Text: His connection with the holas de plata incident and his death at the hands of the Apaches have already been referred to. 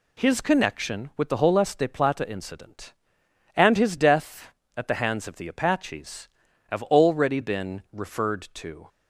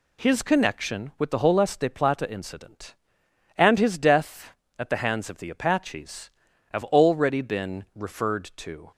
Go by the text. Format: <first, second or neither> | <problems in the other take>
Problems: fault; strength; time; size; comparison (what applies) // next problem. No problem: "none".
neither | none